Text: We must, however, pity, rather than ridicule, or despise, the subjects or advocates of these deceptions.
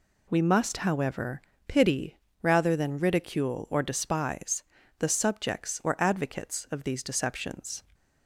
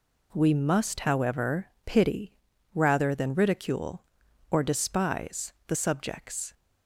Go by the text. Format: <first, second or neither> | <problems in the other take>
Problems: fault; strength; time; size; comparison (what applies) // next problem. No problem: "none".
first | stops before "or advocates of these deceptions"; at 6.5 s